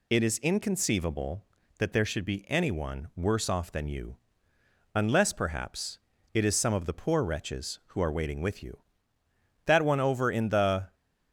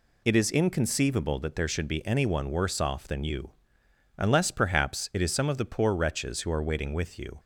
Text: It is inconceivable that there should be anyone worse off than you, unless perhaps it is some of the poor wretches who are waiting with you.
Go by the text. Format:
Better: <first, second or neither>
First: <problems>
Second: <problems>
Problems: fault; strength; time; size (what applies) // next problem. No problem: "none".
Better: second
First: pauses between "perhaps" and "it"; slight; at 5.9 s; 0.36 s long // goes on to say "That one over in the"; noticeable; from 9.6 s on; 1.3 s long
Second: none